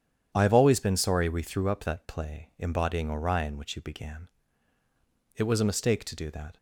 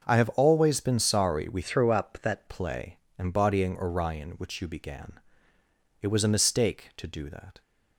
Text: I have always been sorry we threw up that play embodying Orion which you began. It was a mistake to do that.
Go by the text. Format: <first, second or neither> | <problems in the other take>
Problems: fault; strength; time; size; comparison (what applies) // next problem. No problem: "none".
first | starts louder than the rest; noticeable; until 1.0 s; 6 dB // changes voice from "threw" to "that"; from 1.6 to 2.4 s; 0.8 s long // pauses between "play" and "embodying"; slight; at 2.9 s; 0.20 s long